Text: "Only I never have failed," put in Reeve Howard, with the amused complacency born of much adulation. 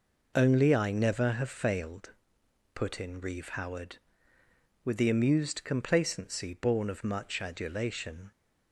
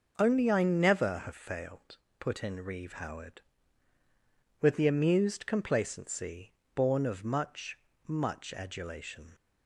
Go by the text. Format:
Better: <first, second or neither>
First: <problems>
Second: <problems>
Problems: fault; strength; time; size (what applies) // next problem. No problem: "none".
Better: first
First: none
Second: pauses between "complacency" and "born"; slight; at 6.5 s; 0.22 s long // says "much" twice; at 8.0 s